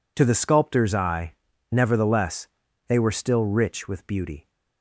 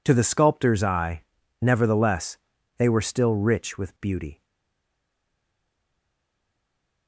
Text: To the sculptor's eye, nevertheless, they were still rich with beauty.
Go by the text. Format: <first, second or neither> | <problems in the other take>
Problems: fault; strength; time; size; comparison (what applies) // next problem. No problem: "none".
first | stays silent after the last word; strong; from 4.4 s on; 2.6 s long